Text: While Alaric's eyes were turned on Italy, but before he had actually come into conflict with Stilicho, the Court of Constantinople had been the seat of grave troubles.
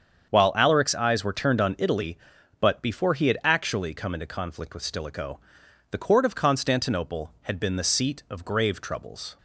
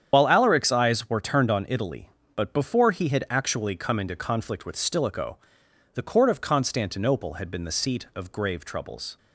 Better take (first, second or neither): first